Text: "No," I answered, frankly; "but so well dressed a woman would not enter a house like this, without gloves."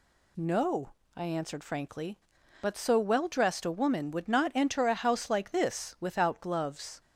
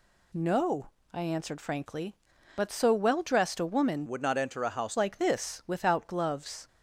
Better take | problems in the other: first | changes voice from "would" to "house"; from 4.0 to 4.9 s; 0.9 s long

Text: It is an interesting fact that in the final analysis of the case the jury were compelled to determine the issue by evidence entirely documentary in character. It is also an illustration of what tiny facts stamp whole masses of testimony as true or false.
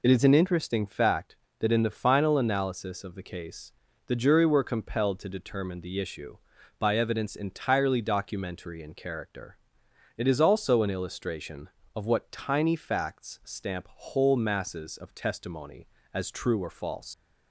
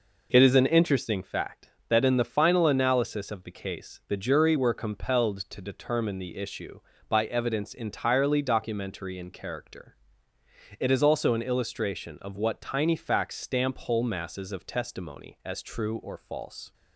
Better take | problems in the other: second | pauses between "case" and "the"; slight; at 3.7 s; 0.34 s long // leaves "false" unfinished; at 17.1 s; 105 ms

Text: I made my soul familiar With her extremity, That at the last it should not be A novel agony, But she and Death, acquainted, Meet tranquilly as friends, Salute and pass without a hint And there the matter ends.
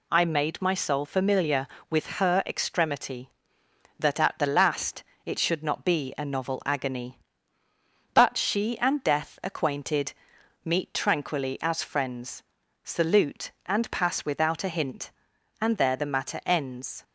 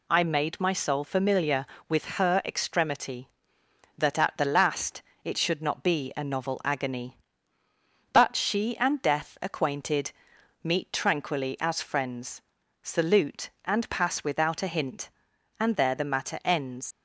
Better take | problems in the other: first | pauses between "last" and "it"; slight; at 5.0 s; 0.22 s long; slight in the first // leaves "ends" unfinished; at 16.9 s; 110 ms

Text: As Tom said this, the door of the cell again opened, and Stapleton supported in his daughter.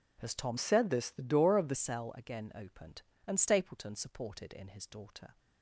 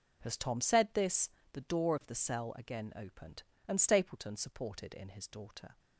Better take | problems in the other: second | changes voice from "said" to "the"; from 0.5 to 1.7 s; 1.2 s long

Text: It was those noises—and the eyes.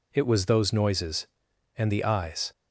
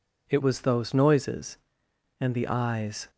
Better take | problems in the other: first | changes voice at "was"; from 0.4 s on; 2.6 s long

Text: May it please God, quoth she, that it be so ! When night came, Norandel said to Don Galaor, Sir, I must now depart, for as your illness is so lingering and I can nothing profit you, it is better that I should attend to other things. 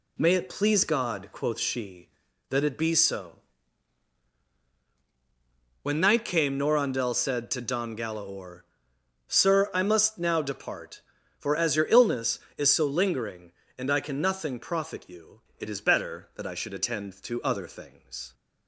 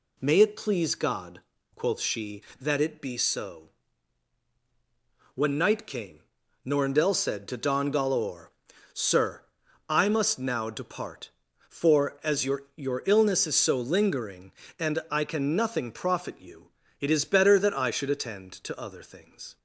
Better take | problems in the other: first | says "your" twice; at 12.7 s

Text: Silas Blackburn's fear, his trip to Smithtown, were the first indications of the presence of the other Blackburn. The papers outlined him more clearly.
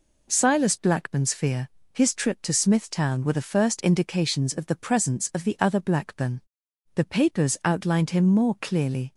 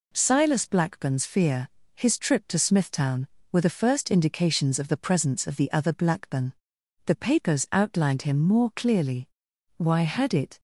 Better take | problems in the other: first | goes on to say "Why had it"; noticeable; from 9.7 s on; 0.82 s long

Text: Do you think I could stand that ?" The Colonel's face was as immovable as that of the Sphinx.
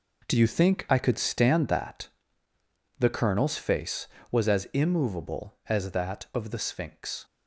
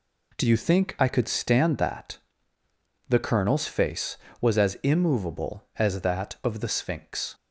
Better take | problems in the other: second | gets quieter; noticeable; throughout; 5 dB

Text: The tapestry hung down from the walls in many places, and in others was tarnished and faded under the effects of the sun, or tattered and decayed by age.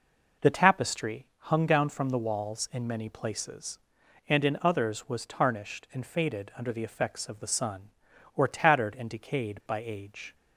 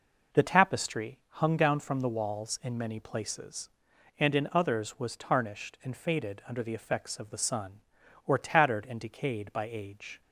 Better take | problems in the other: neither | none

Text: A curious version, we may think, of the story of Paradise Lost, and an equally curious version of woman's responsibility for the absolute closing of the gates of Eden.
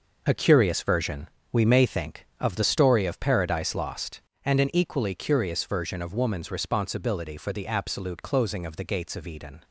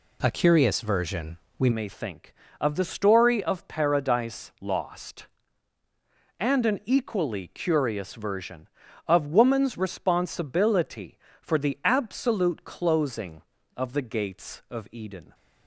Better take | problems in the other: first | changes voice at "may"; from 1.7 s on; 13.6 s long

